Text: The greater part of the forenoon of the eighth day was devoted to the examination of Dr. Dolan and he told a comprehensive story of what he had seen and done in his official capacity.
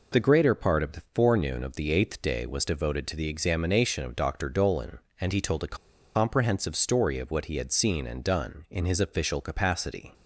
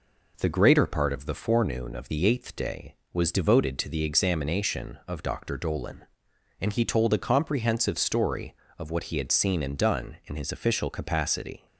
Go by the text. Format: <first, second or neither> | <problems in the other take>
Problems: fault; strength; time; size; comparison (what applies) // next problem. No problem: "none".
second | pauses between "a" and "comprehensive"; at 5.7 s; 0.38 s long